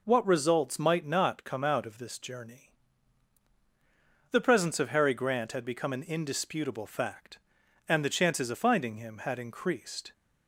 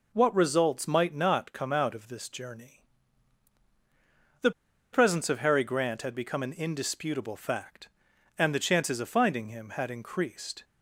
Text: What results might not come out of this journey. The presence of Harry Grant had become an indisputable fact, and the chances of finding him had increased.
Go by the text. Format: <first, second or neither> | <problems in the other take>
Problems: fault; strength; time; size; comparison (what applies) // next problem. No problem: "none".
first | pauses between "The" and "presence"; at 4.5 s; 0.42 s long